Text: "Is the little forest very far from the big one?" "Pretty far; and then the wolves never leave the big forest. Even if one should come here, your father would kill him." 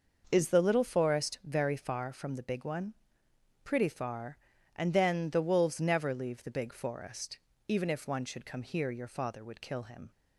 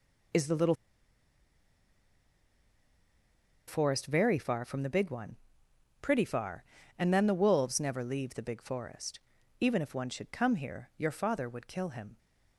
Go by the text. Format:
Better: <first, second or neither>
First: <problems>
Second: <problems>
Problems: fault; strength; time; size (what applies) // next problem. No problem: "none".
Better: first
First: none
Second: pauses between "little" and "forest"; strong; at 0.7 s; 2.9 s long